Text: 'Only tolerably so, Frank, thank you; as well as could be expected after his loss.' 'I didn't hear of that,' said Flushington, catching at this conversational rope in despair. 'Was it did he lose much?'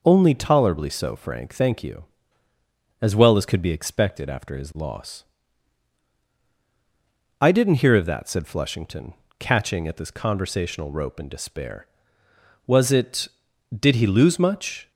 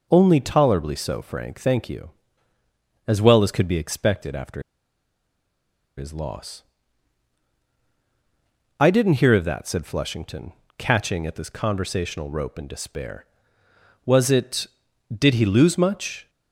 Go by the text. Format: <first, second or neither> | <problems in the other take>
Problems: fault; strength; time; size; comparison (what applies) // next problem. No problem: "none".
first | pauses between "after" and "his"; strong; at 4.6 s; 1.3 s long